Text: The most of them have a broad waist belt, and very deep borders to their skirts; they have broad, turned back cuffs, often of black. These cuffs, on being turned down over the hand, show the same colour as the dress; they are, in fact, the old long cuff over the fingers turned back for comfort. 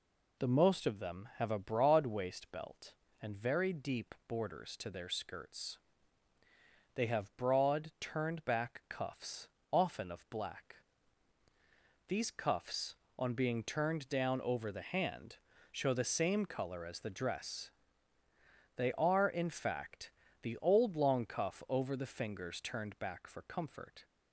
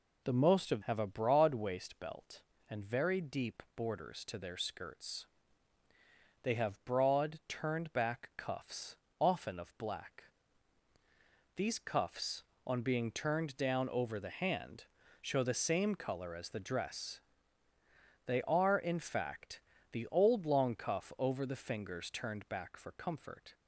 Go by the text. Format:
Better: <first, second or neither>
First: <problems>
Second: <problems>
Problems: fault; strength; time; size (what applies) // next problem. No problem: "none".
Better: first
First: none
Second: skips "them"; at 0.8 s